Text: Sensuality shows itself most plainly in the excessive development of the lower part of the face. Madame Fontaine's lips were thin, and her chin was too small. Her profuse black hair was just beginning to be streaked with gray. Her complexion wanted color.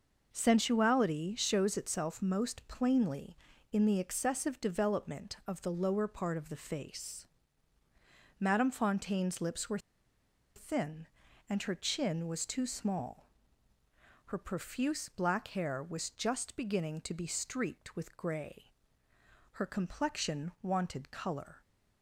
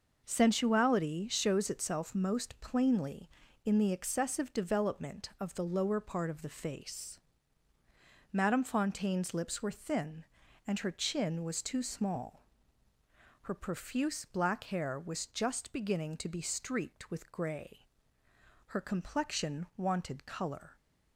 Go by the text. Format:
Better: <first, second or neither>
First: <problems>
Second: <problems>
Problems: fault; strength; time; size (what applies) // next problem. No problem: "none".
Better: second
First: pauses between "were" and "thin"; noticeable; at 9.7 s; 0.77 s long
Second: none